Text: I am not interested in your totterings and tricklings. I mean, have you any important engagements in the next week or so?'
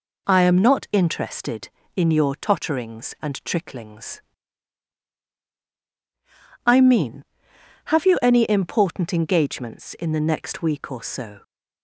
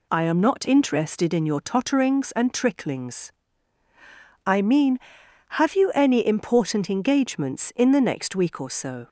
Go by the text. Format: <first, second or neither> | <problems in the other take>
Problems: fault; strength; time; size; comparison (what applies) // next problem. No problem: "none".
neither | none